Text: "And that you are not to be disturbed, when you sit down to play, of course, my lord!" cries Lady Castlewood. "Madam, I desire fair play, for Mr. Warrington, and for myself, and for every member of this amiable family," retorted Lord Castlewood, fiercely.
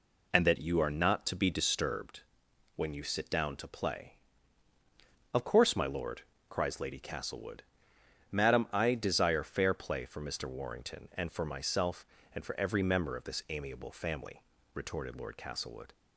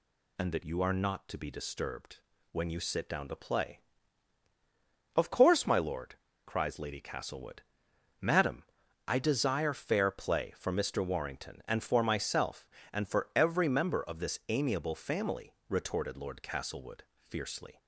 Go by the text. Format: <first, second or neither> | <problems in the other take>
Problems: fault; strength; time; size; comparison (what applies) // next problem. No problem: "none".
second | stops before "fiercely"; at 15.9 s